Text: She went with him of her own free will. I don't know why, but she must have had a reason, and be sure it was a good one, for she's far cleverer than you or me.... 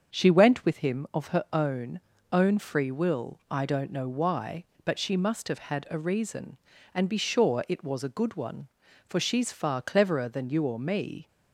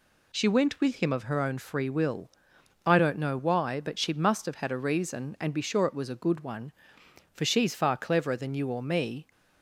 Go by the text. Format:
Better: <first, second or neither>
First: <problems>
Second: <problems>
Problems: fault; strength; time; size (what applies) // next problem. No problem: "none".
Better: second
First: starts louder than the rest; until 1.2 s; 7 dB // says "own" twice; at 2.3 s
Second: none